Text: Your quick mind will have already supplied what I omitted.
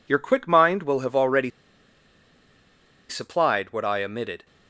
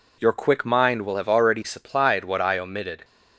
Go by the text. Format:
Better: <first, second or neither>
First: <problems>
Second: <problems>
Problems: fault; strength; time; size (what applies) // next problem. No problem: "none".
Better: second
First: pauses between "already" and "supplied"; strong; at 1.5 s; 1.5 s long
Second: none